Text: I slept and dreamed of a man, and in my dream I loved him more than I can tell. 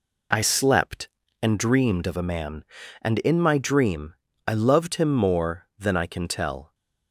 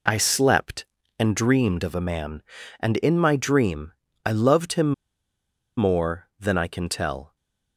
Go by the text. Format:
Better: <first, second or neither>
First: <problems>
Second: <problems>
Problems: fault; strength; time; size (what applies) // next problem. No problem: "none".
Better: first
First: pauses between "dream" and "I"; slight; at 4.1 s; 0.34 s long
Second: pauses between "dream" and "I"; slight; at 3.9 s; 0.34 s long // pauses between "him" and "more"; noticeable; at 4.9 s; 0.84 s long